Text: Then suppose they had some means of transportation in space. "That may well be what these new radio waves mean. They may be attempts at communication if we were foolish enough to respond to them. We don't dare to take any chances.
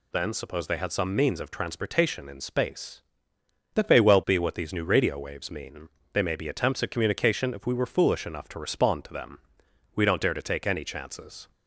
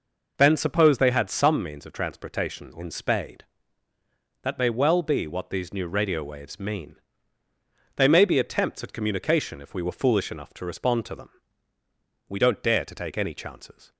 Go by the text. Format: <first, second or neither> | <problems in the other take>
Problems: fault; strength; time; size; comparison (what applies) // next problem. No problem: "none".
first | says "spade" for "space"; at 2.8 s